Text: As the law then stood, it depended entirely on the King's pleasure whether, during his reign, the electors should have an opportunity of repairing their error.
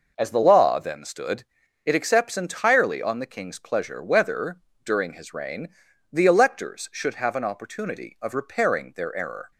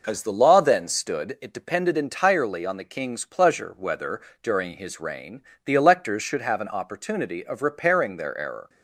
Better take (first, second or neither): second